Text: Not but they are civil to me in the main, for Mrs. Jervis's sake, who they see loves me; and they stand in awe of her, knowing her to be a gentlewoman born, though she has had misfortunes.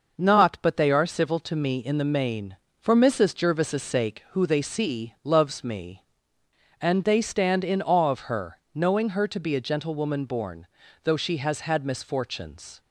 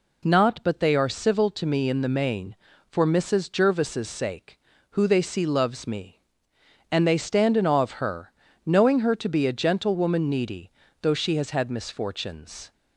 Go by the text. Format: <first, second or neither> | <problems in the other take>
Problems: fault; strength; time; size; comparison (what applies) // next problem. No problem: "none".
first | says "needy" for "born"; at 10.2 s